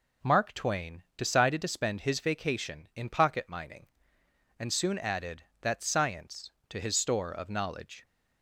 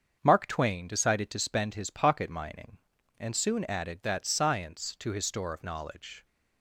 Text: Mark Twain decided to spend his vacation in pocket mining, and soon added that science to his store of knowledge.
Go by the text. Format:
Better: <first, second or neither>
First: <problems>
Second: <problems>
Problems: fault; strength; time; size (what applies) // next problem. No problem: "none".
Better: first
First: none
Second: starts louder than the rest; strong; until 1.2 s; 7 dB // skips "vacation in"; at 1.9 s